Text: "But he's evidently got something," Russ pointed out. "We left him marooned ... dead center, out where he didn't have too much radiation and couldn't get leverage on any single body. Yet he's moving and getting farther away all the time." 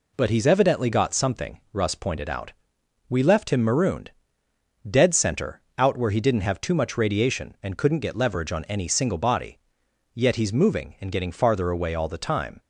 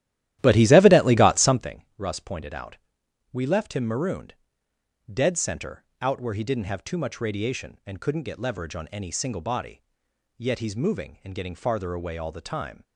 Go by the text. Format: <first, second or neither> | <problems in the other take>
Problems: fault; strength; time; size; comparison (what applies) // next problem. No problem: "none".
first | starts louder than the rest; strong; until 1.7 s; 13.5 dB